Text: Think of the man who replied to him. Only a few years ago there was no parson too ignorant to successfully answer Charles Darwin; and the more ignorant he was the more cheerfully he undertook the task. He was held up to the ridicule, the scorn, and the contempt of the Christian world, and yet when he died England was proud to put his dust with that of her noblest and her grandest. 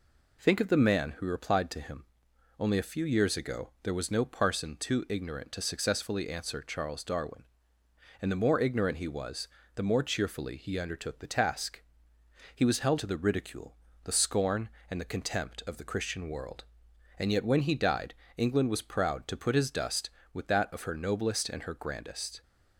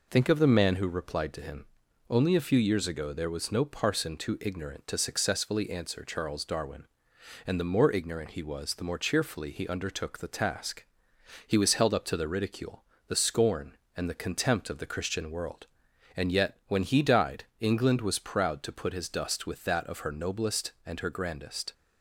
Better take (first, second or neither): second